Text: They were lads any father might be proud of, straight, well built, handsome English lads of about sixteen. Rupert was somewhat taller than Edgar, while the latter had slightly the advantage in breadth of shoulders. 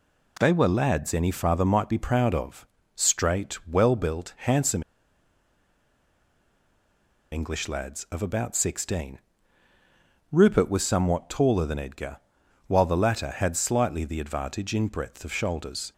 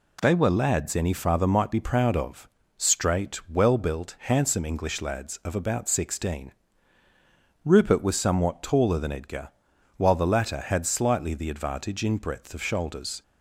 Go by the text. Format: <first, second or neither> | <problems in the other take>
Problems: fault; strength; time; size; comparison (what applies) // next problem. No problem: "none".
second | pauses between "handsome" and "English"; strong; at 4.8 s; 2.4 s long